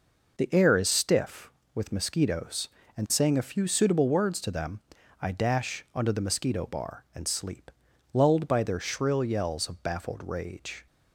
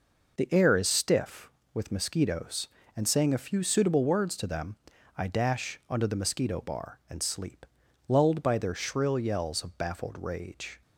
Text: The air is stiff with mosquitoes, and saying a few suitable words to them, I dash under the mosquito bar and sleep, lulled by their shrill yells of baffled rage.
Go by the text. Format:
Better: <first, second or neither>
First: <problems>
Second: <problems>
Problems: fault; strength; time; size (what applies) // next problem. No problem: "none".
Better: neither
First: none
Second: none